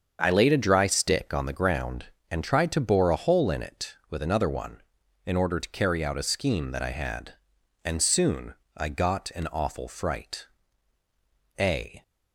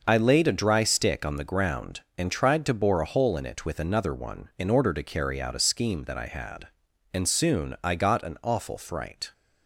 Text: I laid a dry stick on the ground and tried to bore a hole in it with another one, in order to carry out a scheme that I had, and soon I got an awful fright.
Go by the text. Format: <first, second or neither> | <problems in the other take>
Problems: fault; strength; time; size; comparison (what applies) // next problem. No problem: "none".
second | starts louder than the rest; until 1.2 s; 7 dB // pauses between "soon" and "I"; slight; at 8.5 s; 0.24 s long // goes on to say "A"; slight; from 11.5 s on; 0.44 s long